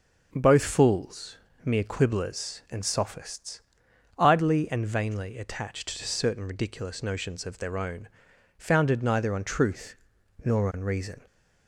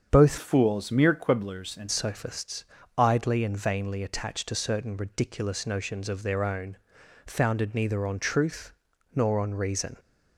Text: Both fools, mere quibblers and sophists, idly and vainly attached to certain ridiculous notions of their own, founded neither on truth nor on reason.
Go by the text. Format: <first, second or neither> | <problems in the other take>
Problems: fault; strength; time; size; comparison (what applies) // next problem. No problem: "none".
first | starts louder than the rest; strong; until 1.1 s; 7.5 dB; also in the first // changes voice from "fools" to "and"; from 0.3 to 1.8 s; 1.5 s long // pauses between "truth" and "nor"; at 8.7 s; 0.42 s long; noticeable in the first